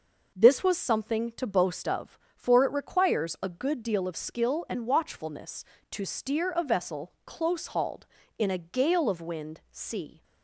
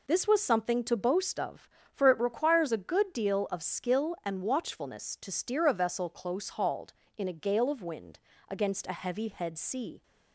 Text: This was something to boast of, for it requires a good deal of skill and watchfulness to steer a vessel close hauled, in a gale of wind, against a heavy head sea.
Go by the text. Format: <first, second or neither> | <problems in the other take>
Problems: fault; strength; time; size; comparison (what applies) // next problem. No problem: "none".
second | skips "against a heavy head"; at 9.6 s